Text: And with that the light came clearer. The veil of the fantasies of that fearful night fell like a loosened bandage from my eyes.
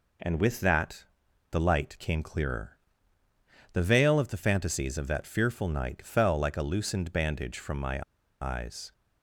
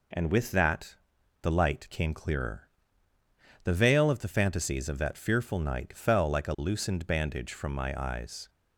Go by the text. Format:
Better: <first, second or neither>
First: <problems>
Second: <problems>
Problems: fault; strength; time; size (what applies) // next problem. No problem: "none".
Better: second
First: pauses between "that" and "the"; noticeable; at 1.0 s; 0.46 s long // pauses between "my" and "eyes"; at 8.0 s; 0.38 s long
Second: pauses between "that" and "the"; noticeable; at 0.9 s; 0.46 s long